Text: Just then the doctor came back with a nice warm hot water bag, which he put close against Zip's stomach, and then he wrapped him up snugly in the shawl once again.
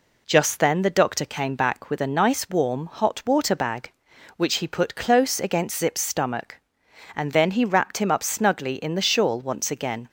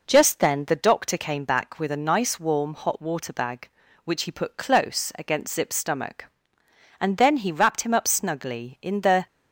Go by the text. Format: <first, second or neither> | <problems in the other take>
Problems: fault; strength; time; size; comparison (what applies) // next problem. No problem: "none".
first | stops before "shawl once again"; at 9.2 s